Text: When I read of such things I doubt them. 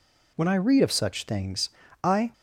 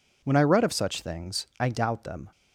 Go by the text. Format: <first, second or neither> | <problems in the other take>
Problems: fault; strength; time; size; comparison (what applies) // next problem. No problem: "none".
second | pauses between "things" and "I"; slight; at 1.6 s; 0.33 s long // stops before "doubt them"; at 2.3 s